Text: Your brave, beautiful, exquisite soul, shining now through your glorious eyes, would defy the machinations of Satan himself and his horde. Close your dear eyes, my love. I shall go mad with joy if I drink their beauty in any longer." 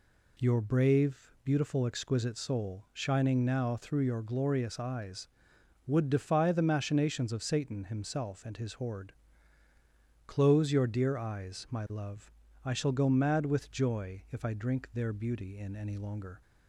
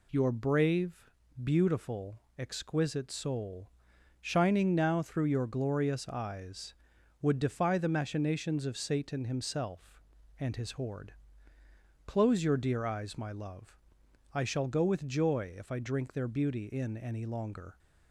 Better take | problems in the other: first | skips "mad"; at 14.8 s

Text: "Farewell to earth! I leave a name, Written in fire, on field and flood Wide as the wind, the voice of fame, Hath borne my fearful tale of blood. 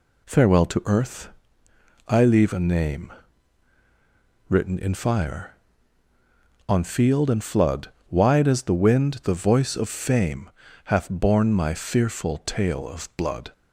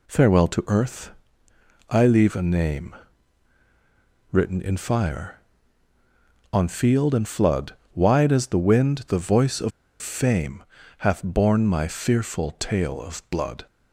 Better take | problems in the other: first | pauses between "flood" and "Wide"; slight; at 7.7 s; 0.18 s long; slight in the first // pauses between "of" and "fame"; slight; at 9.7 s; 0.31 s long

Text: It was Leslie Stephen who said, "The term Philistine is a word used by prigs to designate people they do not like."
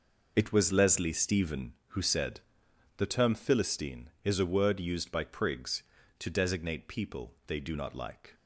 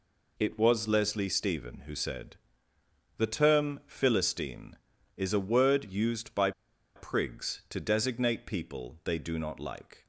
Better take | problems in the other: first | pauses between "by" and "prigs"; at 6.5 s; 0.45 s long

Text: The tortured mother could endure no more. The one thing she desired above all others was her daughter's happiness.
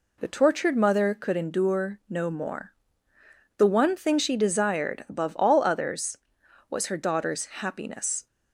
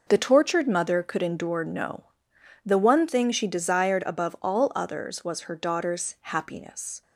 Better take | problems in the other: first | skips "more"; at 2.3 s

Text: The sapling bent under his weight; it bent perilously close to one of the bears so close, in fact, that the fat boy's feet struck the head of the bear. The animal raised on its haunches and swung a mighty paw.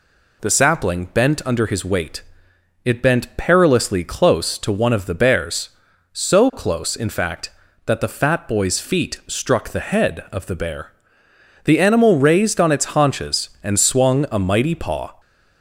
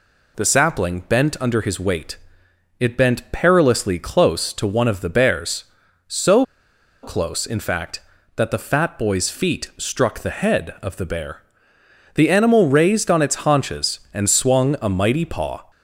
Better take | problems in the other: first | pauses between "so" and "close"; noticeable; at 6.4 s; 0.59 s long

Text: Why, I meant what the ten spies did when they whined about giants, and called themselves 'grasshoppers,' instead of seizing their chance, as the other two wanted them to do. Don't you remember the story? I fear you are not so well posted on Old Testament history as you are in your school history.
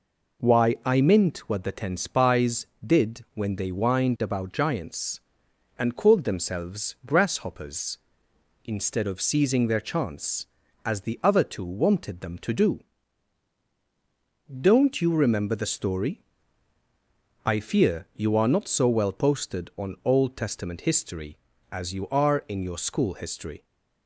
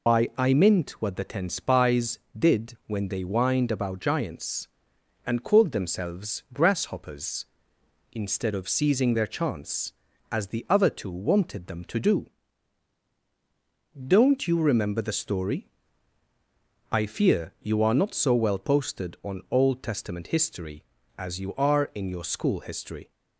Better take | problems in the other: first | loses the start of "Why"; at 0.0 s; 130 ms

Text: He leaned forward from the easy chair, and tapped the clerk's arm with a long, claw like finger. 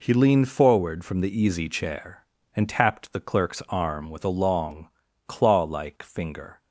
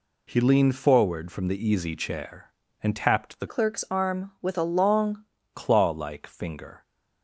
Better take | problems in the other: first | changes voice from "clerk's" to "long"; from 3.4 to 5.2 s; 1.8 s long

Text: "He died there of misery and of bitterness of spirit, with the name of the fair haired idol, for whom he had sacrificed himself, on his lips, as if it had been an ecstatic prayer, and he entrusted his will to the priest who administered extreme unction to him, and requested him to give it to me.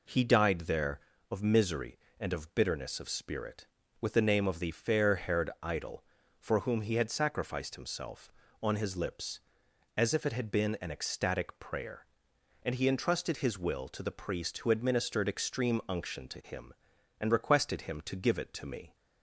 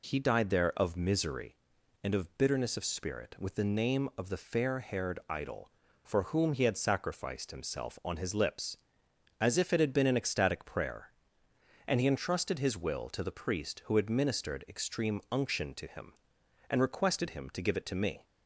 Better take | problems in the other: neither | none

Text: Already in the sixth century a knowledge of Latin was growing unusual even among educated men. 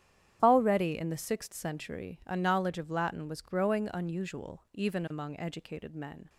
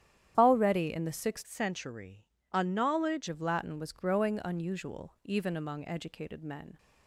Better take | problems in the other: first | starts louder than the rest; strong; until 1.3 s; 10.5 dB; strong in the first // changes voice from "century" to "knowledge"; from 1.4 to 3.2 s; 1.8 s long // pauses between "century" and "a"; slight; at 2.2 s; 0.28 s long

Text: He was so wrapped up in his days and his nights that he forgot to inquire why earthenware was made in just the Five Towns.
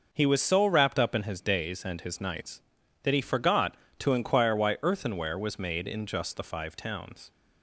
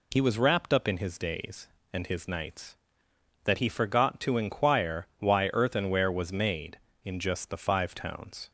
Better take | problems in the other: first | skips "so"; at 0.3 s

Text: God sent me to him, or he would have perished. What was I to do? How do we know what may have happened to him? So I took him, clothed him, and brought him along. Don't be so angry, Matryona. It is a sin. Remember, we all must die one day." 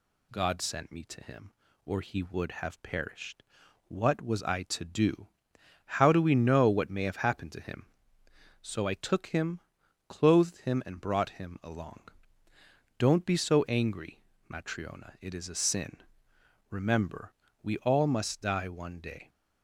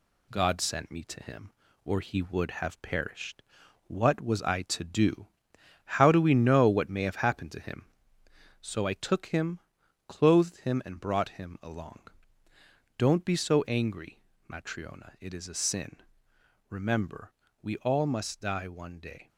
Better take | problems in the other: first | gets quieter; slight; throughout; 2.5 dB

